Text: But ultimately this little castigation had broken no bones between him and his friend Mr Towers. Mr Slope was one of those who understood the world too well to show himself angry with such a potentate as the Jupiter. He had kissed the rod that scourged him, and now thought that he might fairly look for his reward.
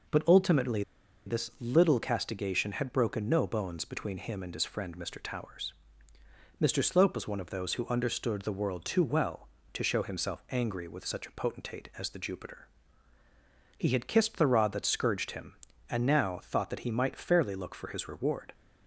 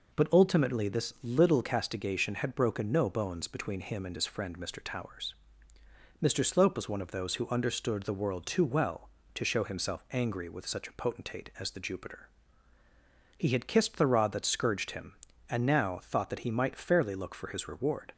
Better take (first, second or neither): second